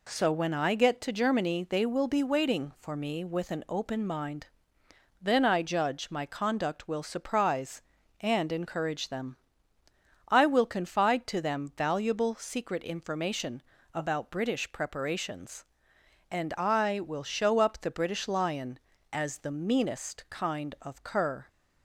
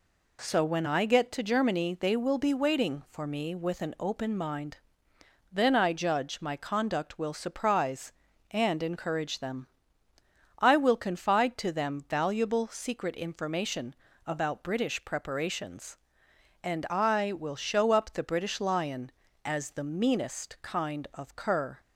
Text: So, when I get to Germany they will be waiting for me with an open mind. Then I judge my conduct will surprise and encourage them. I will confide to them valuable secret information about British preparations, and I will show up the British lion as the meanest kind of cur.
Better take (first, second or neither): neither